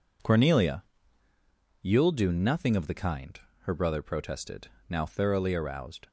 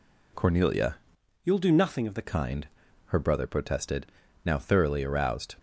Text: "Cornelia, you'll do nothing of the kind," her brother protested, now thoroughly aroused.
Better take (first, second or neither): first